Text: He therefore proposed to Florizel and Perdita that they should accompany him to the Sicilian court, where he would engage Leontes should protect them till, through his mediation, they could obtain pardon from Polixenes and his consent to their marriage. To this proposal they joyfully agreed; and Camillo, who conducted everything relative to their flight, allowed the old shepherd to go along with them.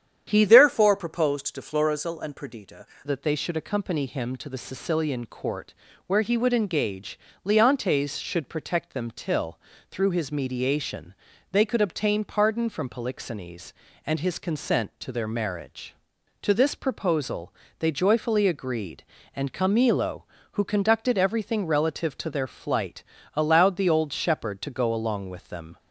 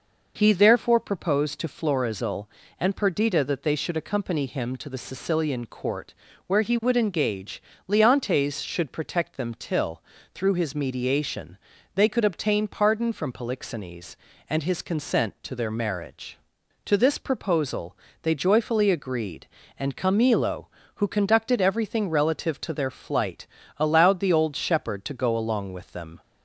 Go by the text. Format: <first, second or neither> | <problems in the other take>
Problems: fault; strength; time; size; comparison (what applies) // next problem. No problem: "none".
second | starts louder than the rest; strong; until 1.3 s; 9 dB // changes voice from "therefore" to "Perdita"; from 0.4 to 2.8 s; 2.4 s long // pauses between "engage" and "Leontes"; slight; at 7.1 s; 0.26 s long; slight in the second // pauses between "proposal" and "they"; slight; at 17.5 s; 0.24 s long; slight in the second